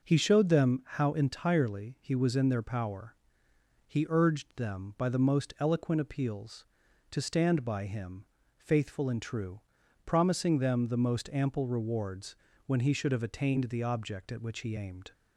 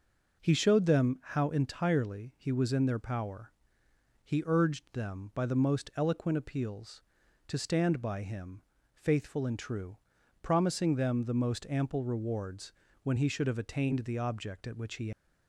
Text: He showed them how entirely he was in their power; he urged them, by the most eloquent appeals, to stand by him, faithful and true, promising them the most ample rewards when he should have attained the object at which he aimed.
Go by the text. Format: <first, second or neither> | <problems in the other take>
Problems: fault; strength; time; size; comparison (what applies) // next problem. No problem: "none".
first | pauses between "rewards" and "when"; slight; at 12.7 s; 0.32 s long; slight in the first // stops before "aimed"; at 15.1 s